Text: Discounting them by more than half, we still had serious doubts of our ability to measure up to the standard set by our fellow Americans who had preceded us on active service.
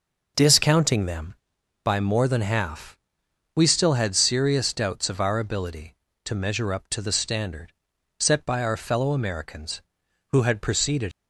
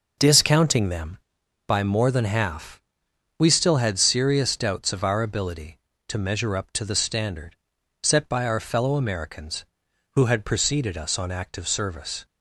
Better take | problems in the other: second | pauses between "standard" and "set"; noticeable; at 7.7 s; 0.48 s long; noticeable in the second // stops before "us on active service"; at 11.1 s

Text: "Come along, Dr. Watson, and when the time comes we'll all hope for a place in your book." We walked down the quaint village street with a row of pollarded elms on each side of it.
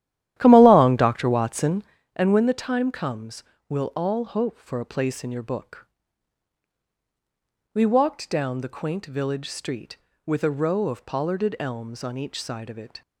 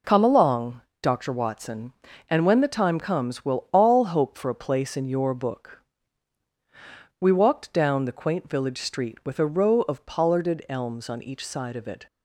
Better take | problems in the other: second | starts louder than the rest; strong; until 2.1 s; 12.5 dB // pauses between "comes" and "we'll"; slight; at 3.4 s; 0.26 s long

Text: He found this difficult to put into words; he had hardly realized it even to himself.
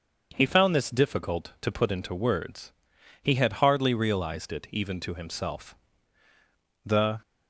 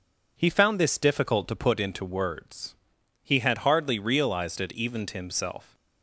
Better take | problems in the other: second | starts louder than the rest; until 1.3 s; 6.5 dB // goes on to say "The"; slight; from 6.8 s on; 0.34 s long

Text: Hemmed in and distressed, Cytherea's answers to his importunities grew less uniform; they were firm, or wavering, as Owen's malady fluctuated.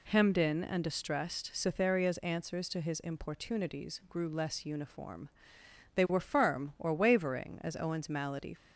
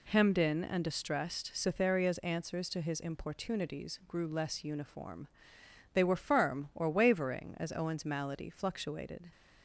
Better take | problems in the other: second | stops before "fluctuated"; at 8.5 s

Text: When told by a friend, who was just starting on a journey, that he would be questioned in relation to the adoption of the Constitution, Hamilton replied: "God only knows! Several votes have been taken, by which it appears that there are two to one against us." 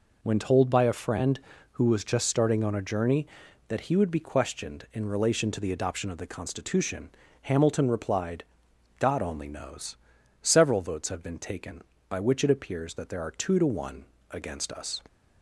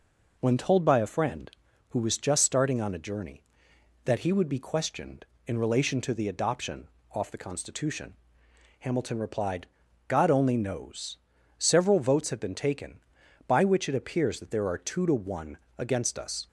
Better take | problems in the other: first | says "off" for "of"; at 7.1 s // pauses between "one" and "against"; slight; at 15.5 s; 0.22 s long; slight in the first

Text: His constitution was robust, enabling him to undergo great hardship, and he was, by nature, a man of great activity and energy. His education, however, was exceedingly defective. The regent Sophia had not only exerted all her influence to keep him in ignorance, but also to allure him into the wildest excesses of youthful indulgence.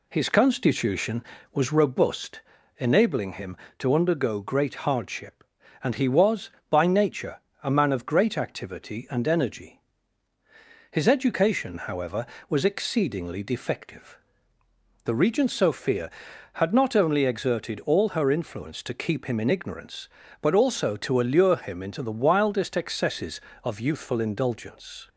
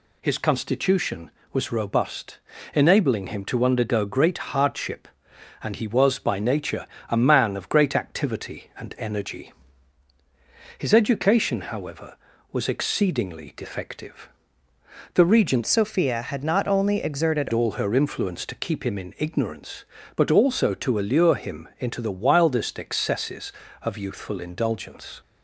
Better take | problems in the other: first | changes voice from "Sophia" to "exerted"; from 15.6 to 17.4 s; 1.8 s long

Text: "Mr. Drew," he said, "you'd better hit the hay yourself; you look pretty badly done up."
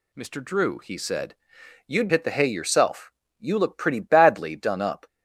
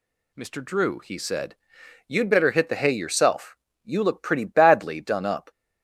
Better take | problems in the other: second | skips "better"; at 2.0 s

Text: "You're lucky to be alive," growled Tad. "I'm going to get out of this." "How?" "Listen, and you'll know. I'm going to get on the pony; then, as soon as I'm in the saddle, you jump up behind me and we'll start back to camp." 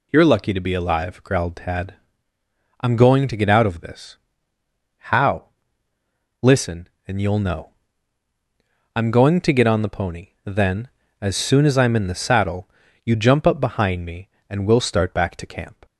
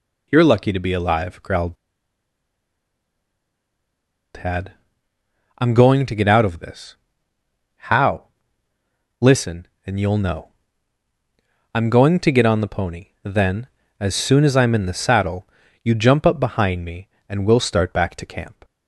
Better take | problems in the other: first | pauses between "growled" and "Tad"; strong; at 1.7 s; 2.6 s long

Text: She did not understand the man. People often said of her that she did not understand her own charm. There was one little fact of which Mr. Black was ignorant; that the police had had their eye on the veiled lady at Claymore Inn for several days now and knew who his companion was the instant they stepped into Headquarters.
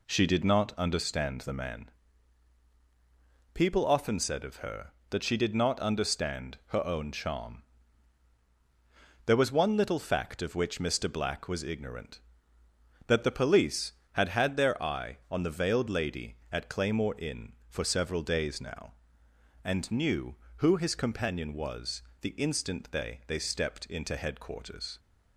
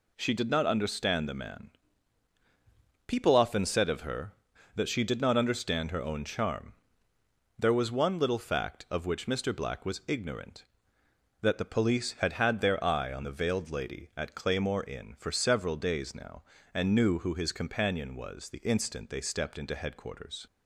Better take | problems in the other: second | pauses between "was" and "the"; slight; at 22.0 s; 0.18 s long // says "they" twice; at 23.2 s

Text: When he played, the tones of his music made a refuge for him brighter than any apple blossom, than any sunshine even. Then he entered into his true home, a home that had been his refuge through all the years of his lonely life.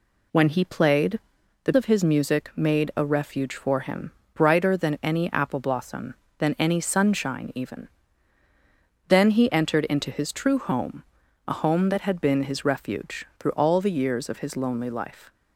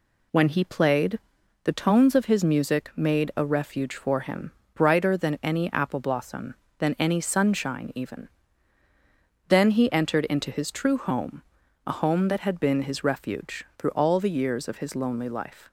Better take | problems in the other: second | skips "tones"; at 1.7 s // pauses between "him" and "brighter"; slight; at 4.1 s; 0.22 s long; slight in the second

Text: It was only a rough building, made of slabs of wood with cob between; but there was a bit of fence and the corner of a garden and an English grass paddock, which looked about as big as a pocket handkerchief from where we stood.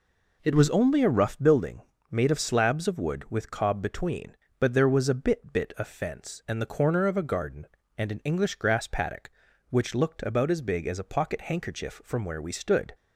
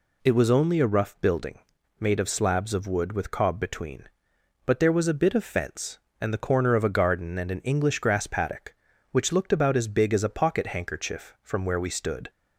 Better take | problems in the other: second | says "bit" twice; at 5.5 s

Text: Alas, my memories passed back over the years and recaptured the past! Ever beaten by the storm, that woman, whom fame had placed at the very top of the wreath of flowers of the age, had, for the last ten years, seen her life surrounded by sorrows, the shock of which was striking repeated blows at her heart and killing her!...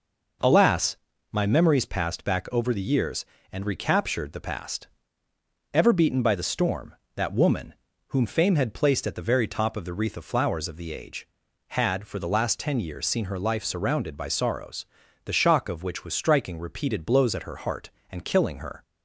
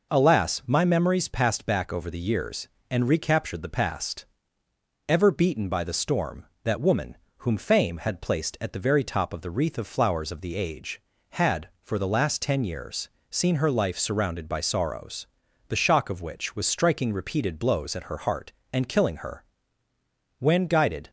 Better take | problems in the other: first | goes on to say "When guided"; noticeable; from 20.3 s on; 0.72 s long

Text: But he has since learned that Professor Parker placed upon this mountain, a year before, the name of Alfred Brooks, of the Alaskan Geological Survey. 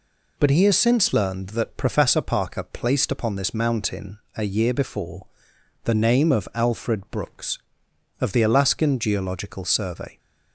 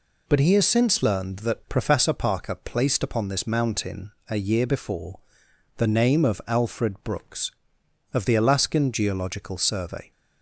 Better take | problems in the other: neither | none

